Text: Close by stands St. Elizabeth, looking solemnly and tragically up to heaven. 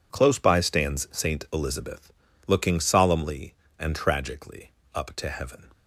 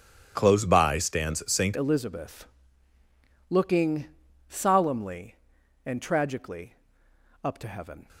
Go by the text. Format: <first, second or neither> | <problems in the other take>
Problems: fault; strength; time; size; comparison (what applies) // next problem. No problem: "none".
first | changes voice at "Elizabeth"; from 1.7 s on; 6.3 s long // pauses between "looking" and "solemnly"; at 4.0 s; 0.42 s long // pauses between "tragically" and "up"; noticeable; at 6.7 s; 0.72 s long; slight in the first